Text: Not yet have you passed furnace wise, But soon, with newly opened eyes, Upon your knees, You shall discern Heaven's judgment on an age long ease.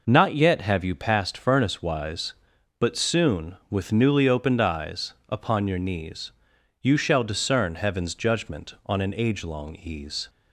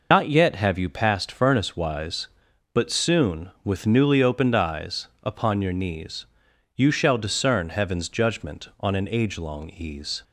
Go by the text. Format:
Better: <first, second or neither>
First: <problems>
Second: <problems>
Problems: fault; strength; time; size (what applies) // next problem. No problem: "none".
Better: first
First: none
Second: loses the start of "Not"; at 0.1 s; 95 ms